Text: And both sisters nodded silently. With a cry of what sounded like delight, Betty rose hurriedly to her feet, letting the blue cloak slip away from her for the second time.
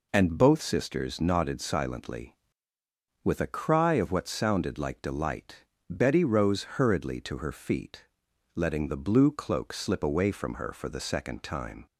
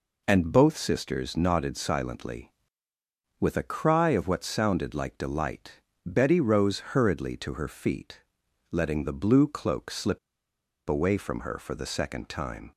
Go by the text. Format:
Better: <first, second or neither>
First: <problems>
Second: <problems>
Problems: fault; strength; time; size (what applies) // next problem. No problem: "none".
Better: first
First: none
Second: pauses between "slip" and "away"; noticeable; at 10.1 s; 0.70 s long